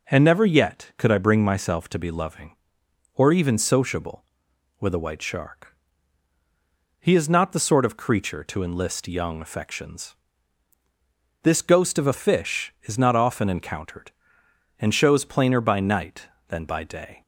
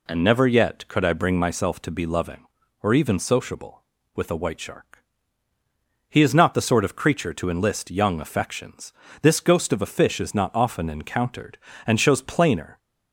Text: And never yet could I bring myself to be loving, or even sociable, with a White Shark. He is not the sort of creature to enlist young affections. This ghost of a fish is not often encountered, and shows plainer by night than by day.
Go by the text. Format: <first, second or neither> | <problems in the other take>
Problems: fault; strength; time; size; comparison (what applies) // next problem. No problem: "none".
first | stops before "by night than by day"; at 12.7 s